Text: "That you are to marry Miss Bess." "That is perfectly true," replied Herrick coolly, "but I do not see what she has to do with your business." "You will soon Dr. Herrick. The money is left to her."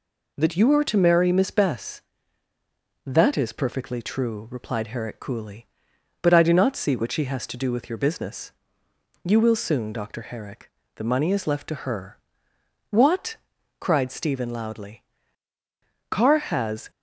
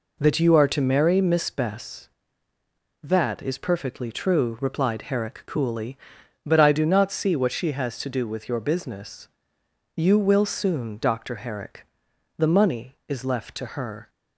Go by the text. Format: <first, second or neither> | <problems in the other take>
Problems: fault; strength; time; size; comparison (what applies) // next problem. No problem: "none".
second | goes on to say "What cried Stephen loudly Carr has"; strong; from 12.8 s on; 4.0 s long